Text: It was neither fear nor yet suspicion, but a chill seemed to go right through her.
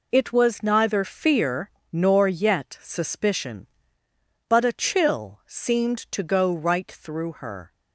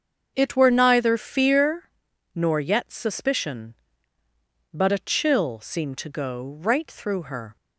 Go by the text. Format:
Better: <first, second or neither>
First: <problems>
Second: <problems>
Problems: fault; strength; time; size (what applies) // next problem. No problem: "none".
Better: first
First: pauses between "fear" and "nor"; slight; at 1.6 s; 0.23 s long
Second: starts louder than the rest; until 1.3 s; 6.5 dB // says "were" for "was"; at 0.5 s // pauses between "fear" and "nor"; at 1.8 s; 0.44 s long